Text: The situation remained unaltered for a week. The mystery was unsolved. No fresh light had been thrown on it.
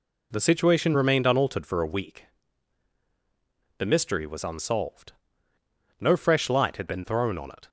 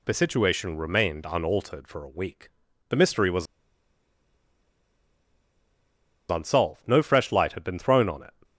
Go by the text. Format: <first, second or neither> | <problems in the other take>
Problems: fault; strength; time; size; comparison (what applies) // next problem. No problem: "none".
first | pauses between "was" and "unsolved"; strong; at 3.4 s; 2.8 s long